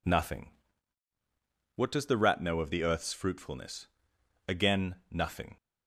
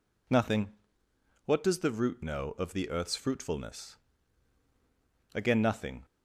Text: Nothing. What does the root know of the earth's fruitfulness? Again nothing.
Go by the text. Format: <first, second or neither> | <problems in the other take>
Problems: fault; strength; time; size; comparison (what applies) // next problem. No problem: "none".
second | says "rat" for "root"; at 2.1 s